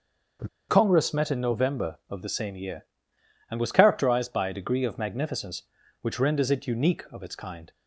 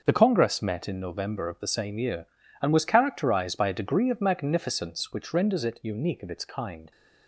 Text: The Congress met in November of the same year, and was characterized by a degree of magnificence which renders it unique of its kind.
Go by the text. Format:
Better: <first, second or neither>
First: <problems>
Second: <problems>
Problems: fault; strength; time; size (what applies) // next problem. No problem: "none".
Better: second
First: starts louder than the rest; until 1.6 s; 6.5 dB // pauses between "The" and "Congress"; slight; at 0.4 s; 0.20 s long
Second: starts louder than the rest; until 1.0 s; 6.5 dB